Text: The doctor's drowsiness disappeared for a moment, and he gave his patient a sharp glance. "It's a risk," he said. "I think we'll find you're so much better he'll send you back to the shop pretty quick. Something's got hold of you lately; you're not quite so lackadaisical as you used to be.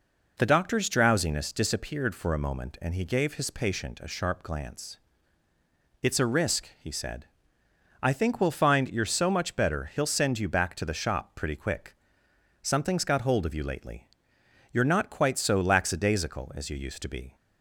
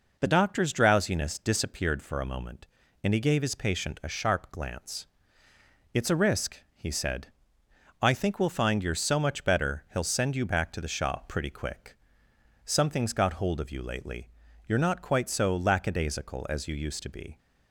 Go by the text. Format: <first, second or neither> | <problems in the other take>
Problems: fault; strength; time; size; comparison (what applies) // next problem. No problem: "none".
neither | none